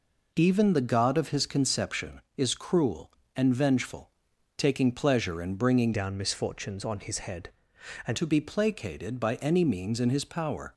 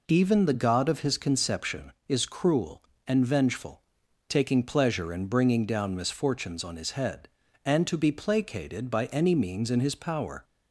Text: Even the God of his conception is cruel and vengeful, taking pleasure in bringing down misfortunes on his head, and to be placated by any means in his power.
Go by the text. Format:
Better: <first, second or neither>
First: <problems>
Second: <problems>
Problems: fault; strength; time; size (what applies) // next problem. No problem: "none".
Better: second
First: changes voice from "down" to "and"; from 5.9 to 8.1 s; 2.2 s long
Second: none